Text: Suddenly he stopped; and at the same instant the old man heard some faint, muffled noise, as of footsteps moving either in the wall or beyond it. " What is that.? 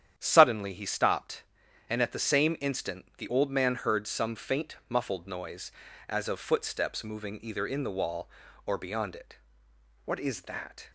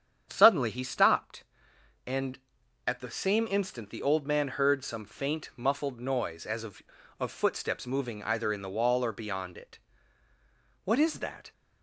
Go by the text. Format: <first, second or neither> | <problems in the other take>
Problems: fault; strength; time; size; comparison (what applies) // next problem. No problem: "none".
first | starts louder than the rest; strong; until 1.3 s; 8.5 dB; strong in the first // says "of" twice; at 7.1 s